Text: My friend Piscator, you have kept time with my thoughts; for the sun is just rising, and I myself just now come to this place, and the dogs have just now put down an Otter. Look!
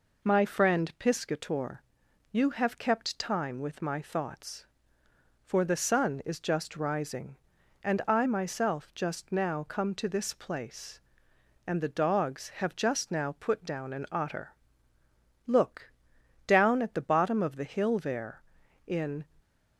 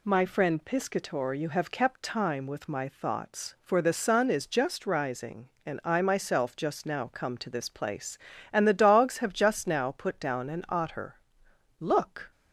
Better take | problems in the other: second | goes on to say "down at the bottom of the hill there in"; strong; from 16.4 s on; 2.7 s long

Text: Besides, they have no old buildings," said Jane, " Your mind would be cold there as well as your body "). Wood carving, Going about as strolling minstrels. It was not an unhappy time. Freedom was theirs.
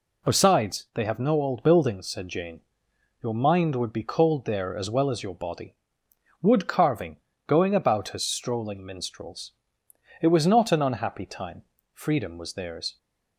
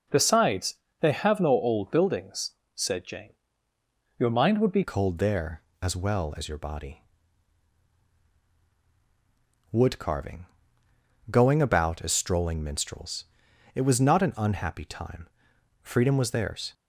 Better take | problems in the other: first | starts louder than the rest; strong; until 1.3 s; 8 dB // changes voice at "cold"; from 4.8 s on; 11.9 s long

